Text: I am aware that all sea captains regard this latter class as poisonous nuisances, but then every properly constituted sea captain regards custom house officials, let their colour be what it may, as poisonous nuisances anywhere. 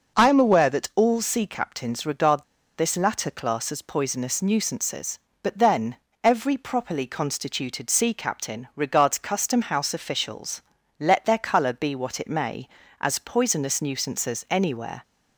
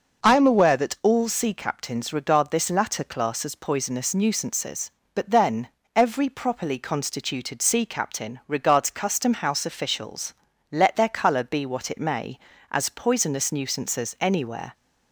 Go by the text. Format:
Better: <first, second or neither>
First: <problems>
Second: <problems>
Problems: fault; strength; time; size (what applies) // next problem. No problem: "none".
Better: second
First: pauses between "regard" and "this"; slight; at 2.4 s; 0.34 s long // pauses between "then" and "every"; slight; at 5.9 s; 0.28 s long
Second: pauses between "then" and "every"; slight; at 5.6 s; 0.28 s long